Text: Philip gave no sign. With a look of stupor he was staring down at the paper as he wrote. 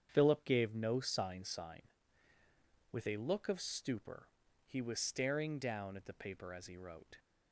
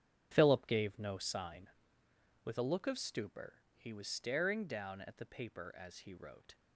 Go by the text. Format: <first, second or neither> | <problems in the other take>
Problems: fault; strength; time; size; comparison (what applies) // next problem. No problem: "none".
second | starts louder than the rest; strong; until 1.1 s; 8 dB; strong in the second // says "sign" twice; at 1.4 s // pauses between "stupor" and "he"; at 4.2 s; 0.38 s long; slight in the second